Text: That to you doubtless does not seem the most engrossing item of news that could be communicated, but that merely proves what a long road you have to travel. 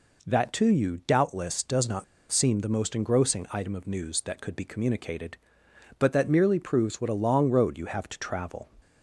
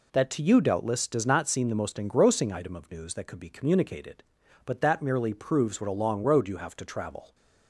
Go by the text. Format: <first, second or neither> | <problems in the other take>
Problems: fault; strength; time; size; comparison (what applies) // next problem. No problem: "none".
second | pauses between "not" and "seem"; slight; at 2.0 s; 0.26 s long